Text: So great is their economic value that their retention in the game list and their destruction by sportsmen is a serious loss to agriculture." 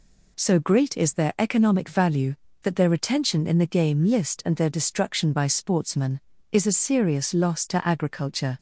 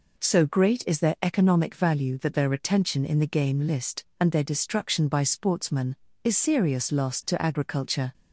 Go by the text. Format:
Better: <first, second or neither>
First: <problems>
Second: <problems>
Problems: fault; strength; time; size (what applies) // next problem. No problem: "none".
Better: first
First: none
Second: skips "a"; at 6.3 s